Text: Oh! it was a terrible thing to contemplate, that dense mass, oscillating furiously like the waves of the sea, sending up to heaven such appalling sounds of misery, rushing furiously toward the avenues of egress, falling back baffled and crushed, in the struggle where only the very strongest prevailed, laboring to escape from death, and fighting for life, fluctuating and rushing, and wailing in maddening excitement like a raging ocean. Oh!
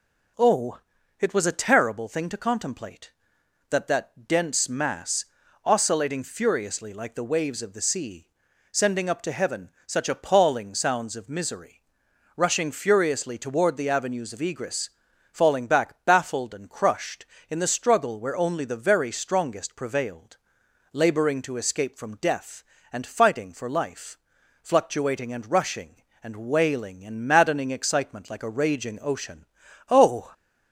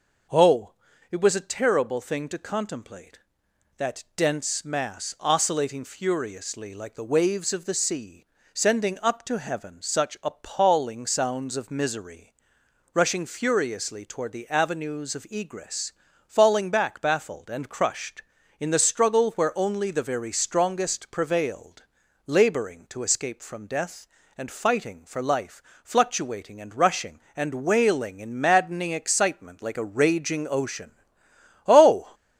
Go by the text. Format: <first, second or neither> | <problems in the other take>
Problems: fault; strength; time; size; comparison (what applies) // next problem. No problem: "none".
second | says "that" twice; at 3.8 s // pauses between "heaven" and "such"; slight; at 9.6 s; 0.16 s long